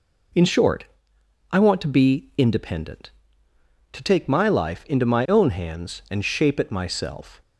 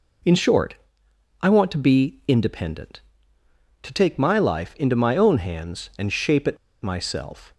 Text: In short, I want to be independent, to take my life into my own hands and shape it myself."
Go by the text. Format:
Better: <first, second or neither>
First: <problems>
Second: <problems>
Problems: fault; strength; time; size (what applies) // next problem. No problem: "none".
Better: first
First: none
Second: pauses between "it" and "myself"; slight; at 6.5 s; 0.27 s long